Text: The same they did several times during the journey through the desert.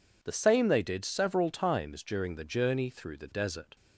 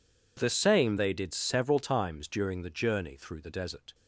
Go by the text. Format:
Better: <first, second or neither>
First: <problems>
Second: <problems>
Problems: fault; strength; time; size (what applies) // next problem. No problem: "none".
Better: neither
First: none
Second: none